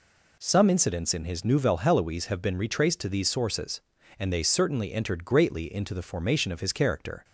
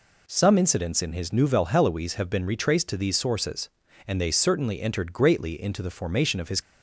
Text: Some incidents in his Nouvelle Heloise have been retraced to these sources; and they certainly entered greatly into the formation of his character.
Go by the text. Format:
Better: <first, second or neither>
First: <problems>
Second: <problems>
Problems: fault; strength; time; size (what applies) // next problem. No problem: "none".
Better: first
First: none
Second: stops before "character"; at 6.6 s